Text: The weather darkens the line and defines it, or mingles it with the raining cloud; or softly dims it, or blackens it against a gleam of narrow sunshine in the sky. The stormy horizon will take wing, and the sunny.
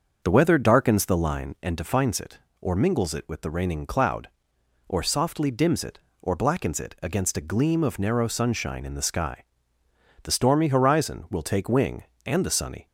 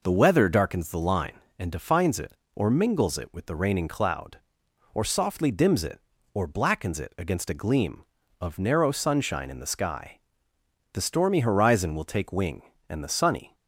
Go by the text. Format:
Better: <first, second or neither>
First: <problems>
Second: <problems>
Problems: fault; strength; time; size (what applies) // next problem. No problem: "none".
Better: second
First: starts louder than the rest; until 1.5 s; 6.5 dB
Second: none